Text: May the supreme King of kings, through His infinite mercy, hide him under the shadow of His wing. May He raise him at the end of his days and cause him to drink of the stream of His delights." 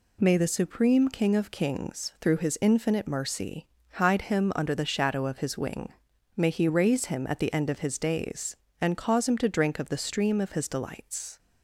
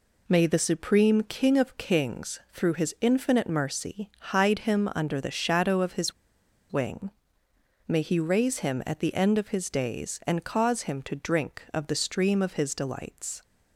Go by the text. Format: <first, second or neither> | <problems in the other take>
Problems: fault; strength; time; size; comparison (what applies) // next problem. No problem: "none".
first | pauses between "His" and "wing"; noticeable; at 6.1 s; 0.59 s long